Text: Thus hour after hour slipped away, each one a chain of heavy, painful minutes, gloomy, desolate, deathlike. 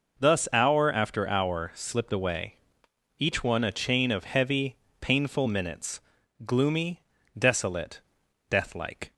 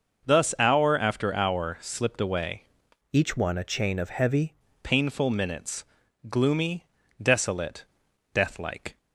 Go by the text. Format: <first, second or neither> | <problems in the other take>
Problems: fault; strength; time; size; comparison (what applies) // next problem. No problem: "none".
first | changes voice from "each" to "heavy"; from 3.1 to 4.5 s; 1.4 s long